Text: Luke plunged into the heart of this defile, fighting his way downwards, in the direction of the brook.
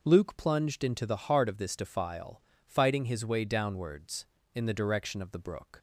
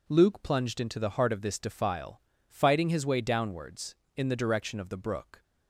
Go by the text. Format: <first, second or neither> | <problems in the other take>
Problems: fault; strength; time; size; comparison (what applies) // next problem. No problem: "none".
neither | none